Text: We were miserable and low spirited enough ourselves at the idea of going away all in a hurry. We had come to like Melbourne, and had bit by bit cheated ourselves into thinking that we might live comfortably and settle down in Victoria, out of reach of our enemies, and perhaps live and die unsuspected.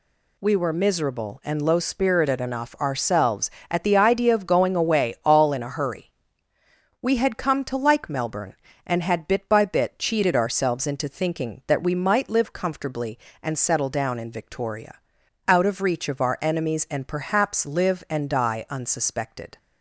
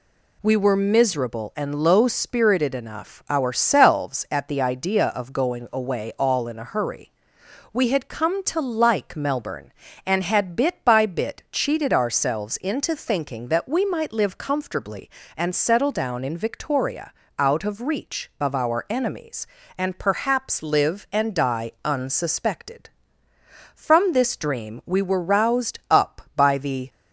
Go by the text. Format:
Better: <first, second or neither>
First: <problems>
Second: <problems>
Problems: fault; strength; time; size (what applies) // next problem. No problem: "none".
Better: first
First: none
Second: goes on to say "From this dream we were roused up by the"; strong; from 23.7 s on; 3.1 s long